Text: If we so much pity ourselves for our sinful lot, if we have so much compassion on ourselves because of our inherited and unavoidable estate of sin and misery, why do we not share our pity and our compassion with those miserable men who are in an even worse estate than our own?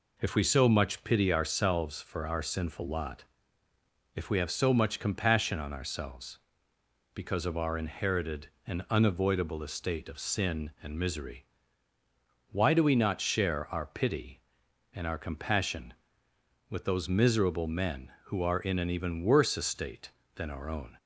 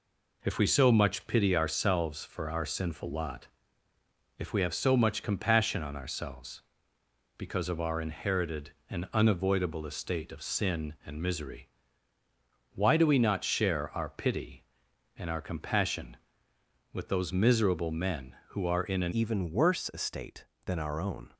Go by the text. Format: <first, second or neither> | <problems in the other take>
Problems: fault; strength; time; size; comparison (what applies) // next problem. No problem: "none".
first | changes voice at "even"; from 19.1 s on; 2.2 s long